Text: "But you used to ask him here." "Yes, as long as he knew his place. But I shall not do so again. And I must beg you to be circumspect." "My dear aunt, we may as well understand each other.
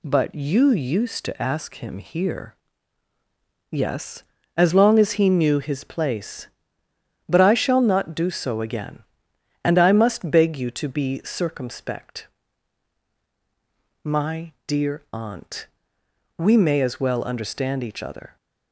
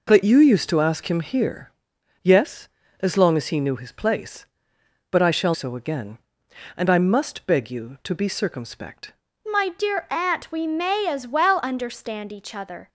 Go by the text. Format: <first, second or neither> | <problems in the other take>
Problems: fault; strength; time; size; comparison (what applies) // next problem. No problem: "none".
first | skips "not do"; at 5.5 s